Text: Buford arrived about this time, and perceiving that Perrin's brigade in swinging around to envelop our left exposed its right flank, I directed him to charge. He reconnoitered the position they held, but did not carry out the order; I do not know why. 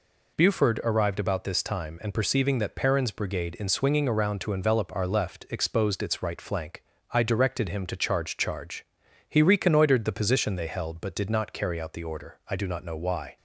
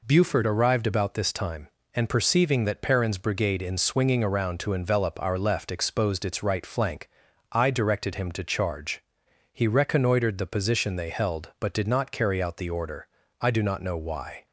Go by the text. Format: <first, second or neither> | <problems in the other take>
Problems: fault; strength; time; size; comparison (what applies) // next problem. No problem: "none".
second | says "charge" twice; at 8.3 s